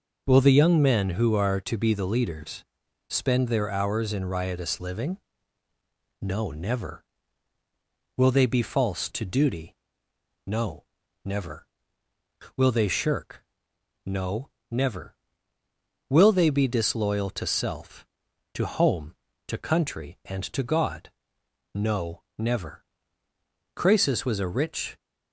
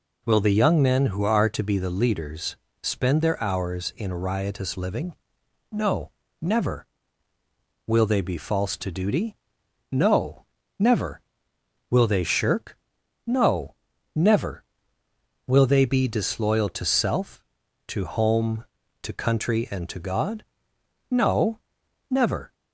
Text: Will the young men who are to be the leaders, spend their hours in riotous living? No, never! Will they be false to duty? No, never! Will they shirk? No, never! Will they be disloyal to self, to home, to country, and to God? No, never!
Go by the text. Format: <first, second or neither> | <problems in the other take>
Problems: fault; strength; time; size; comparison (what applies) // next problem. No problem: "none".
second | goes on to say "Croesus was a rich"; noticeable; from 23.7 s on; 1.2 s long